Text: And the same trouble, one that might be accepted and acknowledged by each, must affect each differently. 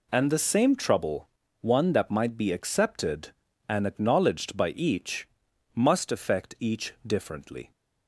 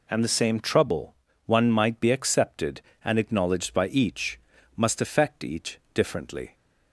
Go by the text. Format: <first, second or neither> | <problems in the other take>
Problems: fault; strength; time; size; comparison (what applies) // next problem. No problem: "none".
first | skips "that"; at 1.7 s